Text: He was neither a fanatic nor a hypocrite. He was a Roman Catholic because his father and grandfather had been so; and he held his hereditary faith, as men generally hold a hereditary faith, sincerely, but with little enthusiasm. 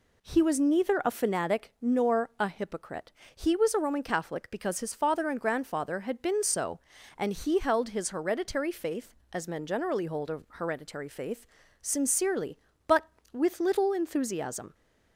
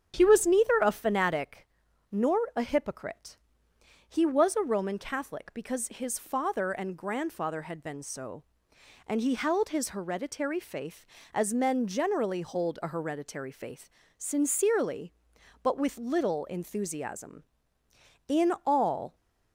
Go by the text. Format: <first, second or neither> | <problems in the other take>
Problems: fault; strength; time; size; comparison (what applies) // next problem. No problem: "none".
first | starts louder than the rest; strong; until 1.1 s; 9 dB // pauses between "fanatic" and "nor"; at 1.6 s; 0.42 s long // pauses between "nor" and "a"; slight; at 2.3 s; 0.16 s long // goes on to say "In all"; noticeable; from 18.2 s on; 0.86 s long